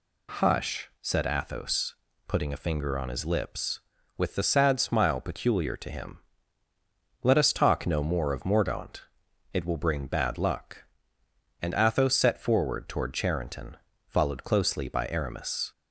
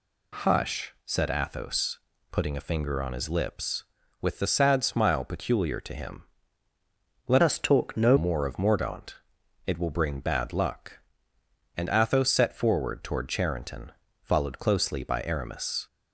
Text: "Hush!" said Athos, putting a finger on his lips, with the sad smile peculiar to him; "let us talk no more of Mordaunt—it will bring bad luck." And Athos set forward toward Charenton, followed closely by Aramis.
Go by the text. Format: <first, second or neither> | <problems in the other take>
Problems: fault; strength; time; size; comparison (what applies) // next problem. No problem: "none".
first | changes voice from "us" to "no"; from 7.4 to 8.1 s; 0.7 s long